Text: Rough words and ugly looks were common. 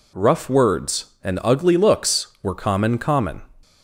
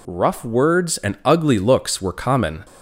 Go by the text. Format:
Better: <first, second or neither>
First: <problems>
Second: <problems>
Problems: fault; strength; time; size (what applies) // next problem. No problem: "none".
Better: second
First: says "common" twice; at 2.9 s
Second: none